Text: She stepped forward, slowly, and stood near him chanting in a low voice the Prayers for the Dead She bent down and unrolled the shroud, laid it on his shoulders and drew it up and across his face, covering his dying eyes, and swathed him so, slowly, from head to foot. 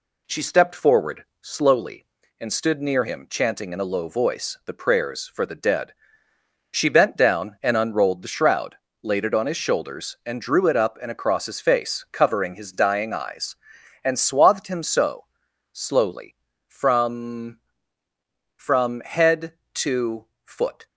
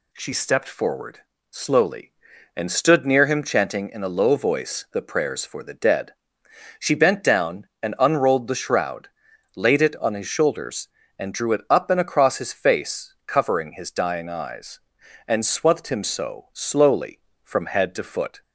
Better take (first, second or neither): second